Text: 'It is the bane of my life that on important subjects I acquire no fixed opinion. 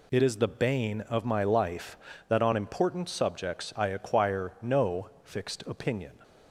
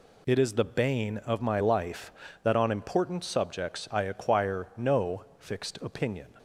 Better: neither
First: pauses between "no" and "fixed"; slight; at 5.0 s; 0.16 s long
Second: pauses between "no" and "fixed"; slight; at 5.2 s; 0.16 s long

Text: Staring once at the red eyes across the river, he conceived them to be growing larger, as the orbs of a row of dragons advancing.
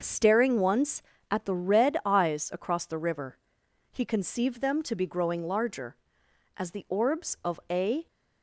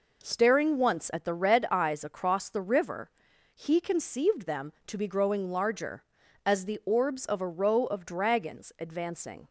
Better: second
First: stops before "row of dragons advancing"; at 8.0 s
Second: none

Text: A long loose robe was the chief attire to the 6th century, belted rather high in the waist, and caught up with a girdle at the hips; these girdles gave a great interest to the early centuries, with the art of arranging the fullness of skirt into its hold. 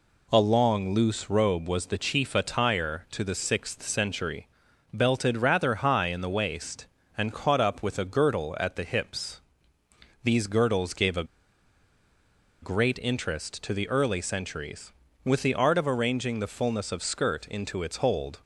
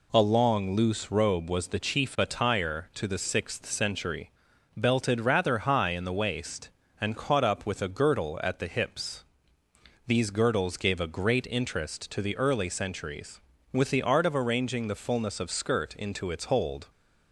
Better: second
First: pauses between "a" and "great"; strong; at 11.2 s; 1.3 s long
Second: none

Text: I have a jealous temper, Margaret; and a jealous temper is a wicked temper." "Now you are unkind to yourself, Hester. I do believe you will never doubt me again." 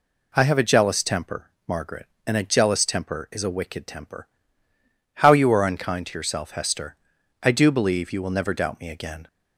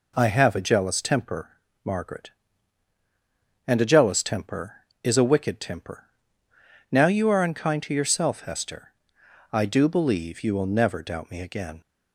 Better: second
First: says "How" for "Now"; at 5.2 s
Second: none

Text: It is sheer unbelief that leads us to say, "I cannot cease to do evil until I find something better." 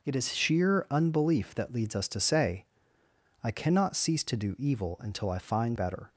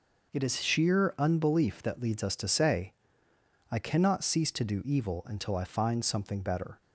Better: second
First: skips "something"; at 5.7 s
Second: none

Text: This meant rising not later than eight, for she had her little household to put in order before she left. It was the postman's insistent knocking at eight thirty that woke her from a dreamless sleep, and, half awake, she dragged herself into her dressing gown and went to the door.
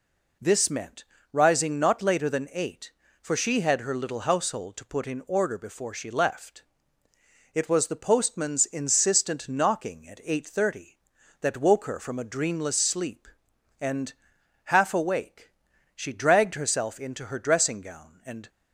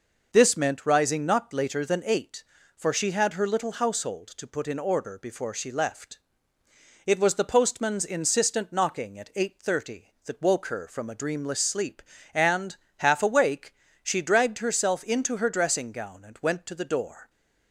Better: second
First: pauses between "meant" and "rising"; slight; at 1.0 s; 0.28 s long // stops before "went to the door"; at 18.4 s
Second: none

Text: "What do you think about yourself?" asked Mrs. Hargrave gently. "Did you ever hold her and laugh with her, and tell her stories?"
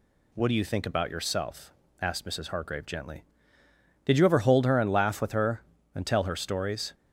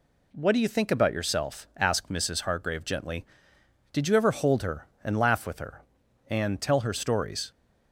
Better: neither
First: none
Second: none

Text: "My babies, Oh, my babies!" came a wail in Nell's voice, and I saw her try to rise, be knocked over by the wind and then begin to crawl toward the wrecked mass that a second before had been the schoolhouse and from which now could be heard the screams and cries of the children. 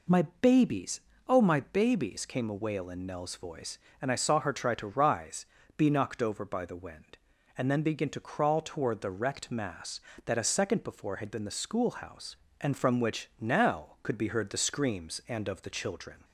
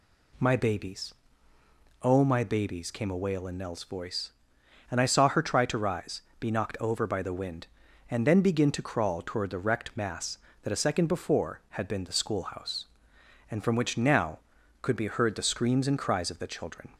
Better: second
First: skips "cries"; at 15.4 s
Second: none

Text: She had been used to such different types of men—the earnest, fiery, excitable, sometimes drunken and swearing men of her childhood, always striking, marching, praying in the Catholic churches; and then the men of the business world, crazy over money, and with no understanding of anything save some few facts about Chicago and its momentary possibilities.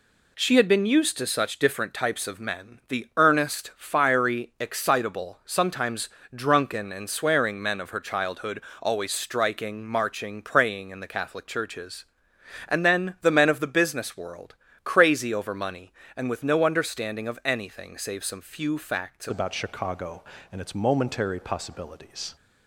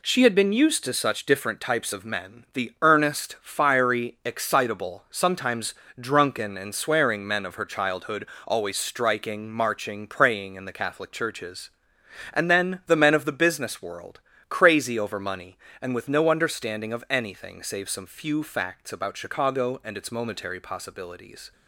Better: second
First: pauses between "sometimes" and "drunken"; slight; at 6.0 s; 0.26 s long // changes voice at "about"; from 19.2 s on; 3.1 s long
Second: pauses between "sometimes" and "drunken"; slight; at 5.7 s; 0.26 s long

